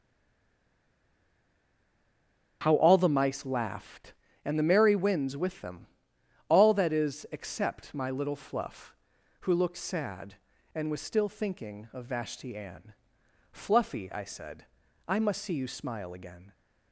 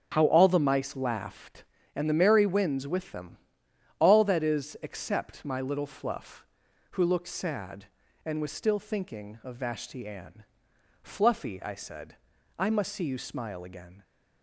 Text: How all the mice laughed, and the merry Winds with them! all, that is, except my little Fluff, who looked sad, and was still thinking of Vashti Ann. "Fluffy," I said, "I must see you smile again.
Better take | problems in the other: second | stays silent before the first word; strong; until 2.6 s; 2.6 s long // starts louder than the rest; until 3.6 s; 6.5 dB; also in the second

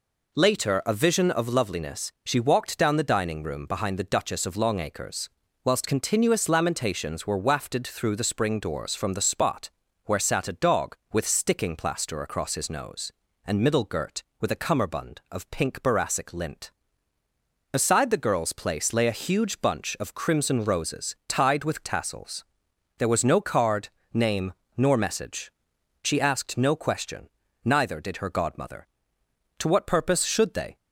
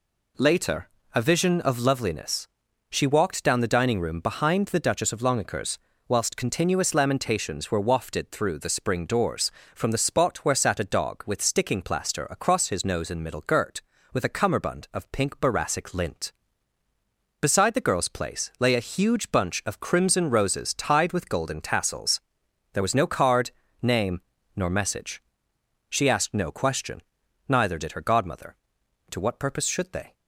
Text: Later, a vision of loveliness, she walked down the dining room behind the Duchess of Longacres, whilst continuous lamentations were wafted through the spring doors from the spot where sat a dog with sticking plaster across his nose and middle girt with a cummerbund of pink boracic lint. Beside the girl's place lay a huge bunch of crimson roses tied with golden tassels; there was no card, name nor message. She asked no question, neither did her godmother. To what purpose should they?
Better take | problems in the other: second | pauses between "spot" and "where"; slight; at 9.7 s; 0.34 s long // skips "golden"; at 21.8 s // pauses between "name" and "nor"; slight; at 24.5 s; 0.26 s long; slight in the second

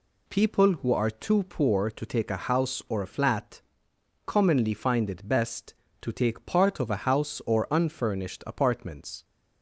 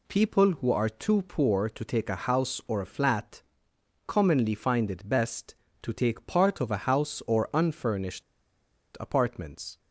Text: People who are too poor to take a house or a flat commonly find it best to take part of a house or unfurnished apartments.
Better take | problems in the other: first | pauses between "flat" and "commonly"; noticeable; at 3.4 s; 0.66 s long; noticeable in the first // pauses between "unfurnished" and "apartments"; noticeable; at 8.2 s; 0.76 s long

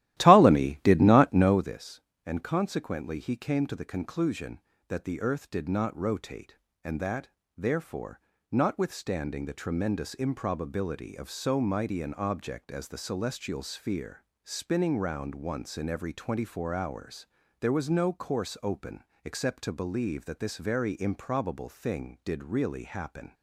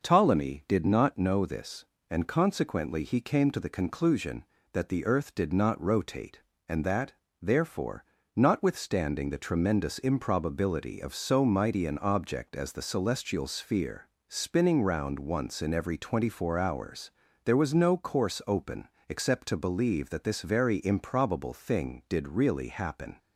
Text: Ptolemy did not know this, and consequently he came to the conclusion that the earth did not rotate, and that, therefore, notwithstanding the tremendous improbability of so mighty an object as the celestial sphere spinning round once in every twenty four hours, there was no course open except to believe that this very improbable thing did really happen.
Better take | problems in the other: second | starts louder than the rest; strong; until 1.7 s; 14.5 dB // pauses between "sphere" and "spinning"; slight; at 14.2 s; 0.20 s long; slight in the second // pauses between "open" and "except"; slight; at 19.0 s; 0.20 s long; slight in the second

